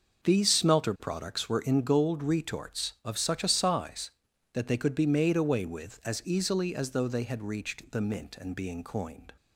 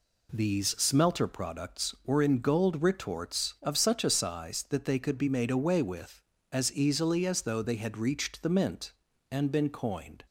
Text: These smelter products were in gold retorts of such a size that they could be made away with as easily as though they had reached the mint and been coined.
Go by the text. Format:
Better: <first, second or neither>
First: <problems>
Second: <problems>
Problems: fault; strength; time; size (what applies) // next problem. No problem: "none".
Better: second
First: says "being" for "been"; at 8.5 s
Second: none